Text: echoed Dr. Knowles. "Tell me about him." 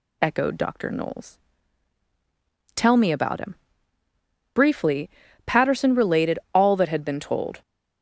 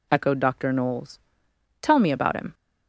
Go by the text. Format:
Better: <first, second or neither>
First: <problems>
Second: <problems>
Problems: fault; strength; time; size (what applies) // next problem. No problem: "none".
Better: second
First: goes on to say "Briefly Patterson related all that had been told"; strong; from 4.5 s on; 3.0 s long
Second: none